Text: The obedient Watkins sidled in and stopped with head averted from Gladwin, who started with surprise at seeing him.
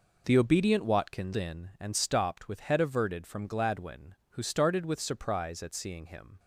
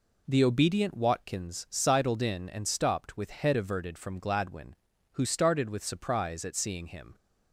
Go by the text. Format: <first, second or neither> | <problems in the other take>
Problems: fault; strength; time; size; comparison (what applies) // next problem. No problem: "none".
second | skips "sidled"; at 1.3 s